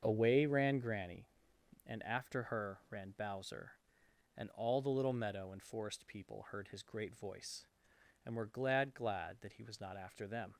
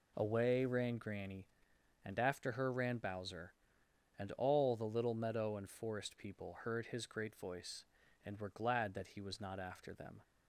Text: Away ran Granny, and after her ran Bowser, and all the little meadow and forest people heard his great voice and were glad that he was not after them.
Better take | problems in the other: second | starts louder than the rest; until 1.0 s; 6.5 dB // says "glad" twice; at 8.9 s

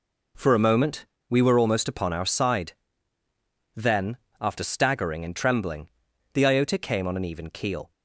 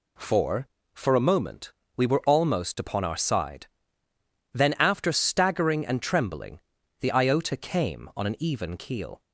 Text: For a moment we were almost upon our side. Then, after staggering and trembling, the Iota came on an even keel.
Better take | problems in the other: first | says "For" twice; at 0.9 s // pauses between "moment" and "we"; slight; at 1.7 s; 0.24 s long; slight in the first

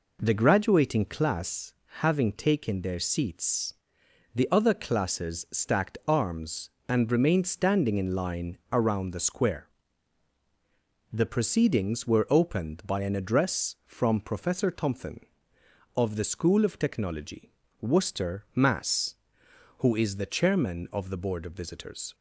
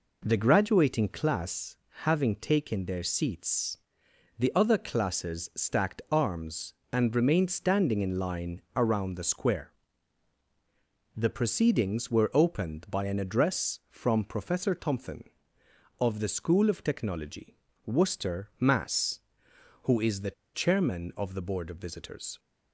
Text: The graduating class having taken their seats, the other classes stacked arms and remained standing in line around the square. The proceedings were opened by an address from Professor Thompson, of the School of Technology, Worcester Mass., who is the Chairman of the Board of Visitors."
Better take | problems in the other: first | pauses between "class" and "having"; slight; at 1.7 s; 0.28 s long; slight in the first // pauses between "the" and "Chairman"; slight; at 20.3 s; 0.22 s long

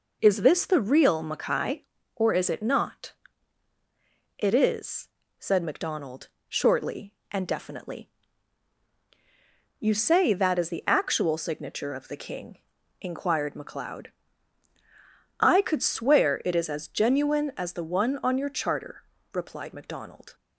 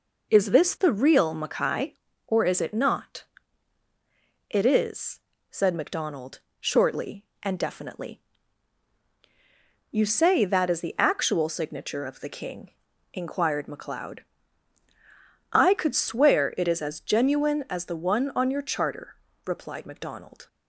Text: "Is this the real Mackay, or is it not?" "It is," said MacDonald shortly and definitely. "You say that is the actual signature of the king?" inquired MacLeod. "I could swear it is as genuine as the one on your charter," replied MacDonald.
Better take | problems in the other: neither | pauses between "MacDonald" and "shortly"; slight; the same in both

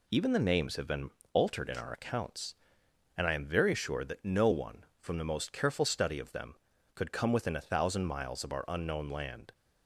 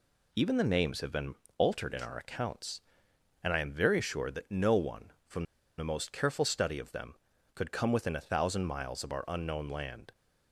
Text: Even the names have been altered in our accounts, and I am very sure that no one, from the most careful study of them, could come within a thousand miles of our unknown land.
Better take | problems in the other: first | pauses between "been" and "altered"; slight; at 1.3 s; 0.22 s long; slight in the first // pauses between "from" and "the"; slight; at 5.4 s; 0.34 s long

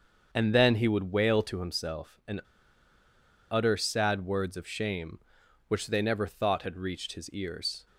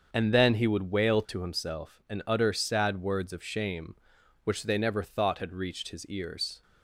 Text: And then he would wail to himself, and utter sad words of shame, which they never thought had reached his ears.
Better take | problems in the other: second | starts louder than the rest; until 1.3 s; 7 dB; also in the second // pauses between "and" and "utter"; at 2.3 s; 1.1 s long

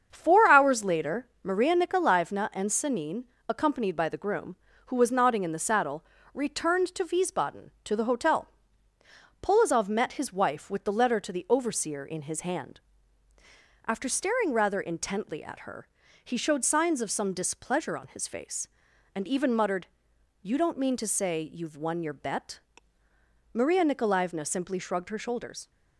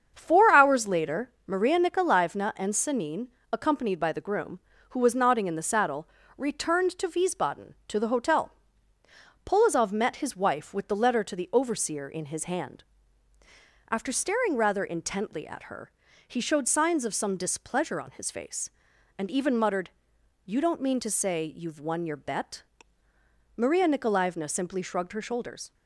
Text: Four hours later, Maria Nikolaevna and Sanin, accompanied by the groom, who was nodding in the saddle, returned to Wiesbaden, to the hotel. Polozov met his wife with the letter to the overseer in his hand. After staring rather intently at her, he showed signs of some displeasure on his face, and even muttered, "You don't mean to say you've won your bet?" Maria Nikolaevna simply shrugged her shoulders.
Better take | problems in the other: neither | starts louder than the rest; strong; the same in both

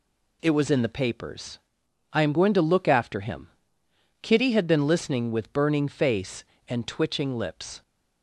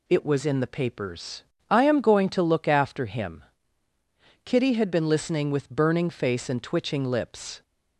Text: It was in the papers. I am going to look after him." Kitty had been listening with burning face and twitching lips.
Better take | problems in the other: neither | none

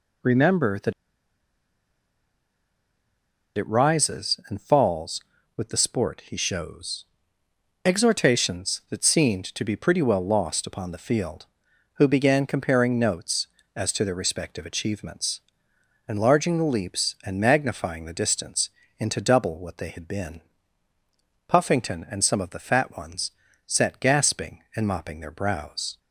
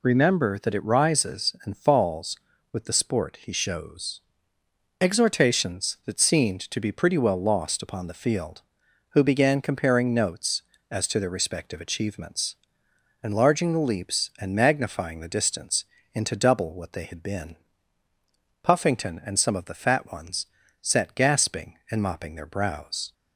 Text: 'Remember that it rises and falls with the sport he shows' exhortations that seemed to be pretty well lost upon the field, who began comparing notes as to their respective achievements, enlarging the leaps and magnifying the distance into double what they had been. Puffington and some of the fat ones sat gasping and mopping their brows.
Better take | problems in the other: second | pauses between "that" and "it"; strong; at 0.9 s; 2.6 s long // pauses between "shows" and "exhortations"; noticeable; at 7.0 s; 0.80 s long; noticeable in the second // pauses between "distance" and "into"; slight; at 18.7 s; 0.28 s long; slight in the second // pauses between "ones" and "sat"; slight; at 23.3 s; 0.34 s long; slight in the second

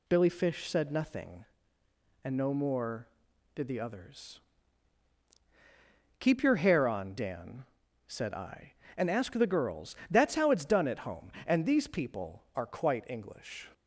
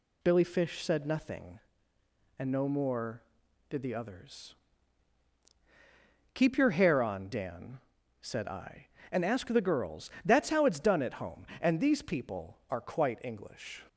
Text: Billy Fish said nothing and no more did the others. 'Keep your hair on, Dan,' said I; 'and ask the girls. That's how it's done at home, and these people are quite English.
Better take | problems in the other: neither | none

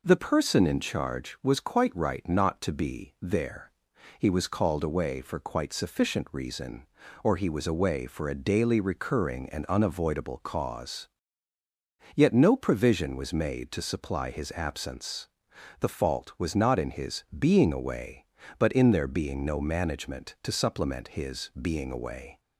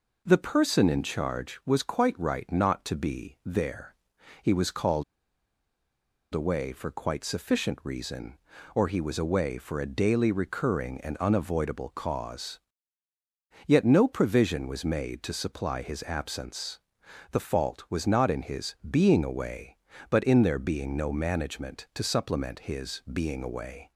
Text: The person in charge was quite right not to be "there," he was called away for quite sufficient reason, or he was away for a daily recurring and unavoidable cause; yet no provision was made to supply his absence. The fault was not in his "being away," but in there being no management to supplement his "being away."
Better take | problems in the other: first | pauses between "called" and "away"; strong; at 5.0 s; 1.2 s long

